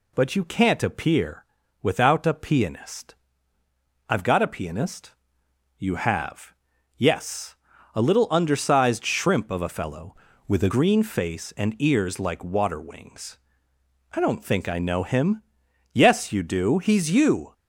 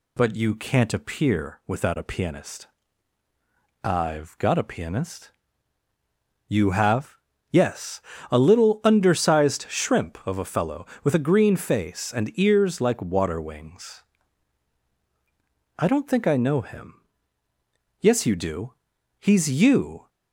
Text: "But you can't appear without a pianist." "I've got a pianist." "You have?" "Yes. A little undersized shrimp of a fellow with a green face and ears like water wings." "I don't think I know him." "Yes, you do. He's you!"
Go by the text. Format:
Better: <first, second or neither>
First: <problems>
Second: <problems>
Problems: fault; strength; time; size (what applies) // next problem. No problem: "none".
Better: second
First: pauses between "appear" and "without"; at 1.4 s; 0.38 s long // changes voice from "with" to "a"; from 10.4 to 10.7 s; 0.3 s long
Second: none